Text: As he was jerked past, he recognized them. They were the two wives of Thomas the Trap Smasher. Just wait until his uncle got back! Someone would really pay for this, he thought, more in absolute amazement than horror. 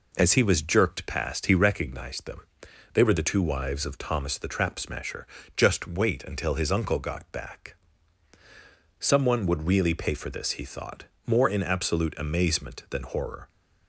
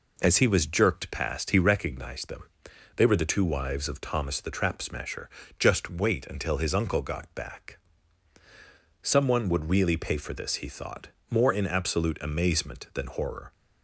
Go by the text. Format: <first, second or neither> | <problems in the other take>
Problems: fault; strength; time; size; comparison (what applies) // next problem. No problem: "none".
neither | none